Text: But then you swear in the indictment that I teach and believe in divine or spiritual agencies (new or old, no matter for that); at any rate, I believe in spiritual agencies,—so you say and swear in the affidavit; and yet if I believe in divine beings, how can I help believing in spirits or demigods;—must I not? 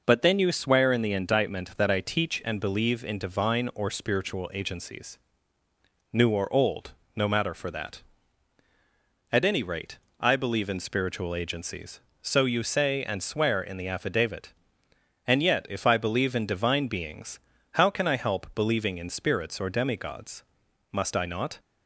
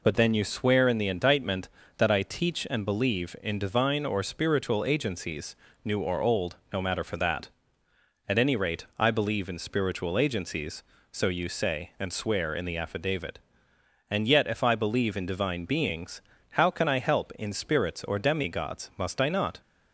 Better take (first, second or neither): first